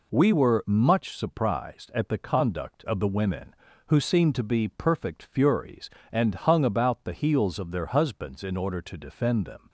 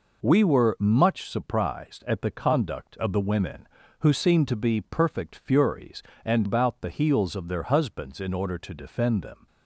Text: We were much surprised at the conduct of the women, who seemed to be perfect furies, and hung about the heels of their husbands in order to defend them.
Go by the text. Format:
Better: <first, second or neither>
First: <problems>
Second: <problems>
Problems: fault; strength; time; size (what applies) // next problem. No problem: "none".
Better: first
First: none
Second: skips "hung"; at 6.4 s